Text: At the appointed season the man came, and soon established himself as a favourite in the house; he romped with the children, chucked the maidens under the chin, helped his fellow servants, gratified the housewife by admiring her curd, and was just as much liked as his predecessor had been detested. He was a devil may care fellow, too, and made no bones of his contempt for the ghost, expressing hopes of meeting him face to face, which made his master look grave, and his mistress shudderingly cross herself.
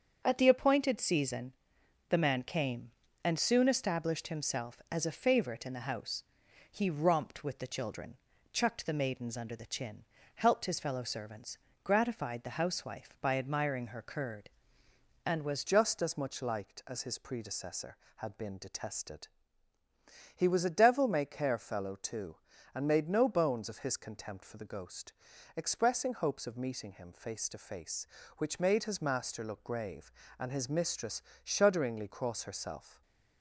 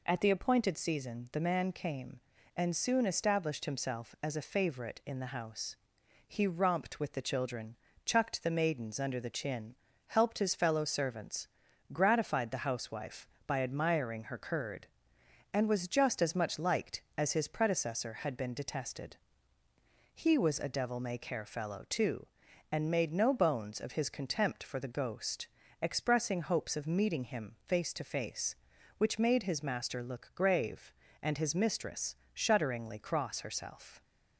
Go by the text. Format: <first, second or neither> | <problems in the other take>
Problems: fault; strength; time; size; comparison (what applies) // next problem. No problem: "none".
second | starts louder than the rest; strong; until 1.2 s; 7 dB // pauses between "season" and "the"; noticeable; at 1.5 s; 0.56 s long // changes voice at "just"; from 15.6 s on; 17.4 s long // pauses between "mistress" and "shudderingly"; slight; at 31.2 s; 0.20 s long; slight in the second